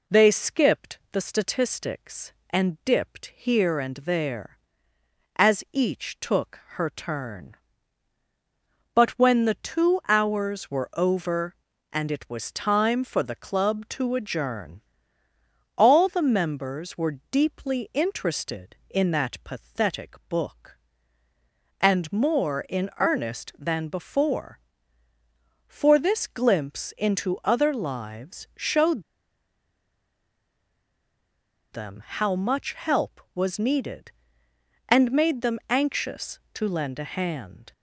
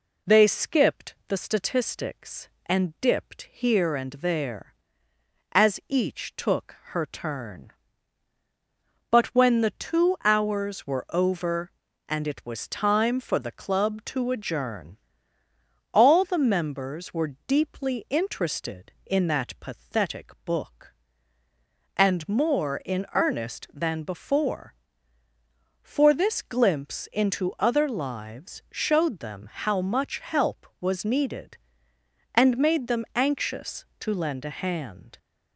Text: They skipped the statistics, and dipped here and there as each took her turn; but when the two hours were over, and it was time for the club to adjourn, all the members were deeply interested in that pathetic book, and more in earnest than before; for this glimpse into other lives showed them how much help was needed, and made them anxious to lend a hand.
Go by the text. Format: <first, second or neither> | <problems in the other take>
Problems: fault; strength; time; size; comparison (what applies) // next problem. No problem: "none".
second | pauses between "showed" and "them"; strong; at 29.0 s; 2.6 s long